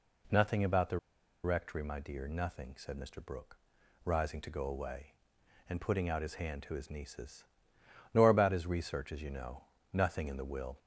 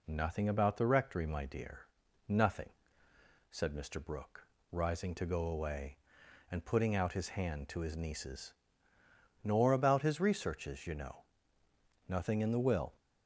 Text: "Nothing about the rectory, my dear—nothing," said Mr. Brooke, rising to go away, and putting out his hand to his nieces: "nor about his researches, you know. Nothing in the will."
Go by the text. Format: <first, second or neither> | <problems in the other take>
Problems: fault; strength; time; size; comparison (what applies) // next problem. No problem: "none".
second | pauses between "the" and "rectory"; noticeable; at 0.9 s; 0.46 s long